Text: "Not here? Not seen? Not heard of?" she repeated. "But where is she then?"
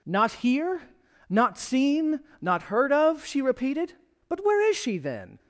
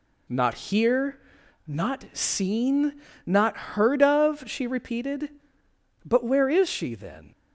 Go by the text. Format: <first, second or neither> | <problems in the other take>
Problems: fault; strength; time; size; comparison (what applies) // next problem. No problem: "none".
neither | none